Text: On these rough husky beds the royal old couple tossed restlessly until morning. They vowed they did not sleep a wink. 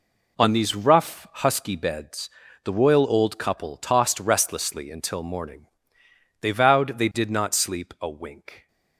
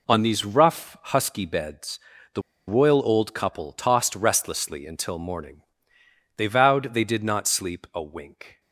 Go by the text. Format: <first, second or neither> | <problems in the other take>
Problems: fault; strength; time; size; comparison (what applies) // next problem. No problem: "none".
first | pauses between "beds" and "the"; slight; at 1.9 s; 0.36 s long; slight in the first // pauses between "the" and "royal"; slight; at 2.4 s; 0.26 s long